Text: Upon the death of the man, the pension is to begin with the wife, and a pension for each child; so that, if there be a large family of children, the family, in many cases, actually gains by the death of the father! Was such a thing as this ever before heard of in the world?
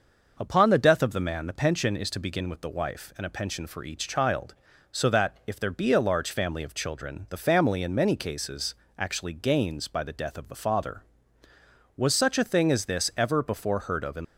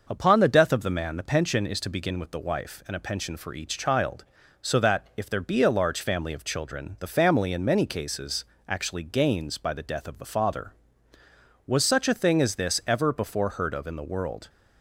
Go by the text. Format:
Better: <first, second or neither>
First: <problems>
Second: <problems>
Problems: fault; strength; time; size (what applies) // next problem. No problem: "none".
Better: second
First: stops before "the world"; at 14.2 s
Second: none